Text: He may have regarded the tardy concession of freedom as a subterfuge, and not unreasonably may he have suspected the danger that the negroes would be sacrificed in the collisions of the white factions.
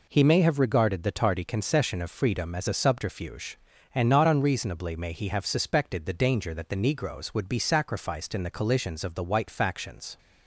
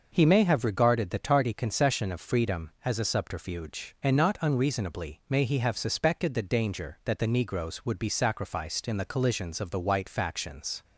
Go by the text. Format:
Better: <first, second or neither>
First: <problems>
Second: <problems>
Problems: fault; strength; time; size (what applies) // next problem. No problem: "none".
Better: neither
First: none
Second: none